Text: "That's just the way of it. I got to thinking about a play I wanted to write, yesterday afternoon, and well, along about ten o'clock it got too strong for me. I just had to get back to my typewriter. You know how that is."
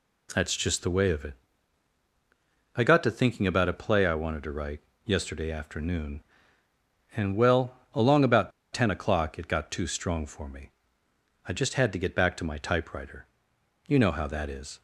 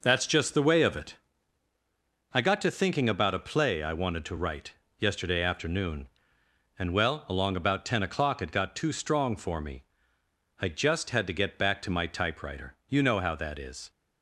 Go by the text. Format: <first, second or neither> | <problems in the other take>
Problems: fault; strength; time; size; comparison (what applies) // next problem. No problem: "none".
second | pauses between "about" and "ten"; slight; at 8.5 s; 0.22 s long